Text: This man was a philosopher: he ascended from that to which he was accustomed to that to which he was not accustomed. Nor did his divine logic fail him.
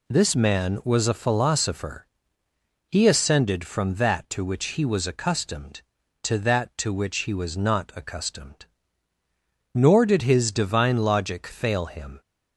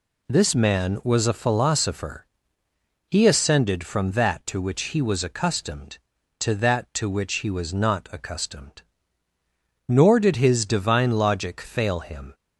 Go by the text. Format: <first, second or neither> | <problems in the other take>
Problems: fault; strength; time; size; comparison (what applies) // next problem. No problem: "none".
neither | none